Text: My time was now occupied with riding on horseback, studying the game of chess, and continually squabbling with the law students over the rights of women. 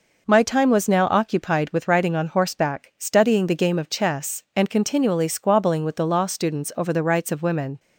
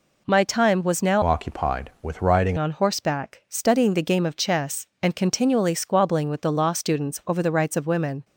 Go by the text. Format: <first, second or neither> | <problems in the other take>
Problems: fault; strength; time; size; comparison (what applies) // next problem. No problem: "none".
first | changes voice from "occupied" to "riding"; from 1.2 to 2.5 s; 1.3 s long